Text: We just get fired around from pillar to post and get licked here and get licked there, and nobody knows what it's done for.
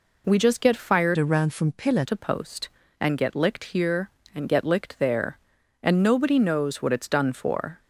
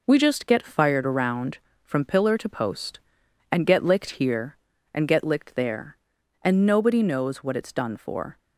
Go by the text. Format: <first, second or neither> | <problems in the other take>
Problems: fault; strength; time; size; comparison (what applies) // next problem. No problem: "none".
second | changes voice from "around" to "pillar"; from 1.1 to 2.0 s; 0.9 s long